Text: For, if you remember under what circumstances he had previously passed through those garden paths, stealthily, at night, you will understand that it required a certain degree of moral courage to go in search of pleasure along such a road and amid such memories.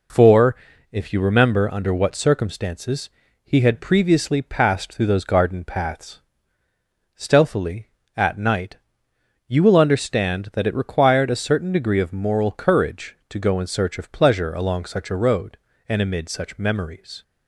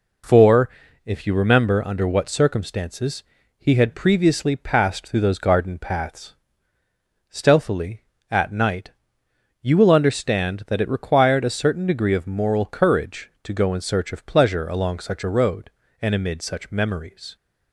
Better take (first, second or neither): neither